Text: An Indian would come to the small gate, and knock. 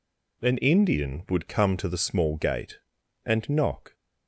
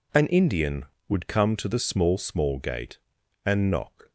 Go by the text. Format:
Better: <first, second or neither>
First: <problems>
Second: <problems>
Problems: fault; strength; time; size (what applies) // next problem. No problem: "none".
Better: first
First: none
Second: says "small" twice; at 2.1 s